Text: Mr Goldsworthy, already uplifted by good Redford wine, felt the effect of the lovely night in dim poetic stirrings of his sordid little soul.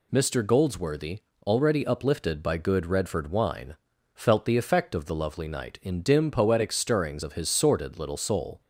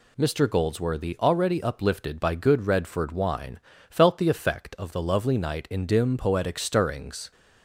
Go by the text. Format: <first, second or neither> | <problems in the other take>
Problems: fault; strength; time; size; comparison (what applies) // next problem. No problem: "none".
first | stops before "of his sordid little soul"; at 7.3 s